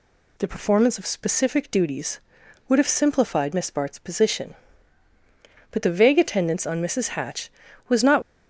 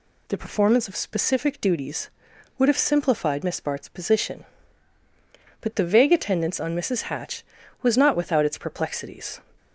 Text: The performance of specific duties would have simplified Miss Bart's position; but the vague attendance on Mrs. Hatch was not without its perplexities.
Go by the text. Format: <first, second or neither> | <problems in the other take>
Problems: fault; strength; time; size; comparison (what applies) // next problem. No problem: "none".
second | stops before "without its perplexities"; at 8.2 s